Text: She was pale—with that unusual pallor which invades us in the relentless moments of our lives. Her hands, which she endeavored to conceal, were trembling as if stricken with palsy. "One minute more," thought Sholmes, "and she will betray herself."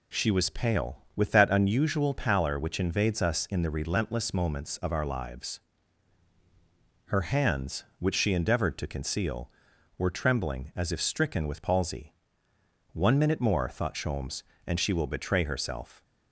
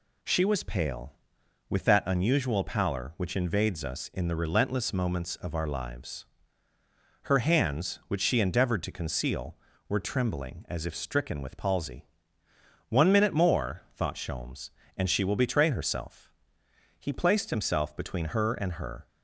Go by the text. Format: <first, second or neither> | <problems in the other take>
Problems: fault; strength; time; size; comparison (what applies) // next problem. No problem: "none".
first | goes on to say "He placed himself between her and her"; strong; from 16.9 s on; 2.0 s long